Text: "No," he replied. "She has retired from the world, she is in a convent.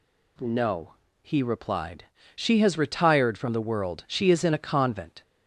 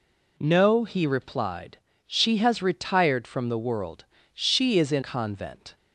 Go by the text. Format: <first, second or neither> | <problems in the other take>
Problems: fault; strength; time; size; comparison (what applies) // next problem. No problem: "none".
first | skips "a"; at 5.0 s